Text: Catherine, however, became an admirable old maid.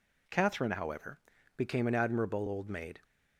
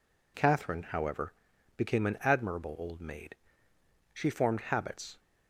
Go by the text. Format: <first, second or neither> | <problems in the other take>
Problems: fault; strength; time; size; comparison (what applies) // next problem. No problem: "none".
first | goes on to say "She formed habits"; noticeable; from 4.1 s on; 1.0 s long